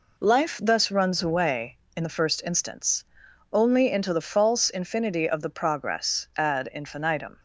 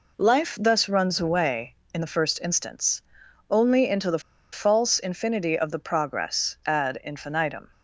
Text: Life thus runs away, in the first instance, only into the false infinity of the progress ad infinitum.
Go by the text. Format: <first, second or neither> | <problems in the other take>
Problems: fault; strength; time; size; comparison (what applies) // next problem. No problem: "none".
first | pauses between "the" and "false"; slight; at 4.2 s; 0.32 s long